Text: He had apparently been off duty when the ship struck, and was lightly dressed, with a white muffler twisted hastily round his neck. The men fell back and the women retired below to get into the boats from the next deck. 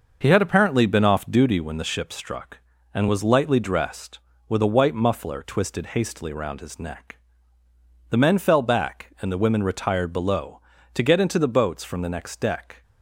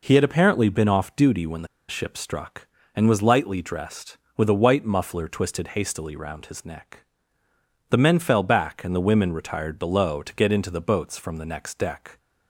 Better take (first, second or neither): first